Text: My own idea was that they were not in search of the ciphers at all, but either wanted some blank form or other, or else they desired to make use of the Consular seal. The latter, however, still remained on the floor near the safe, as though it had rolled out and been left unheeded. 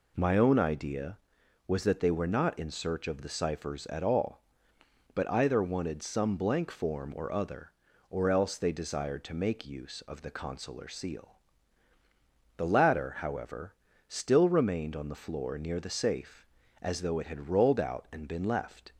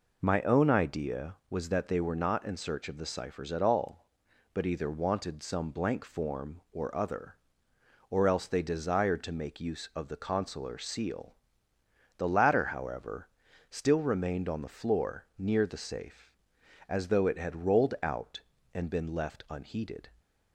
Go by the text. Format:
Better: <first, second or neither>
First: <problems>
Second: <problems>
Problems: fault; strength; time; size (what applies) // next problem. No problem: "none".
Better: second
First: stops before "unheeded"; at 18.9 s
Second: none